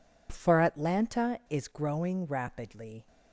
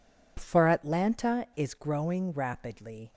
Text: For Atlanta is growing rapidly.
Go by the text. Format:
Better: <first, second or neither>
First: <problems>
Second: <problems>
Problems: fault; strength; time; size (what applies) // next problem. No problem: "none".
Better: neither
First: none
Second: none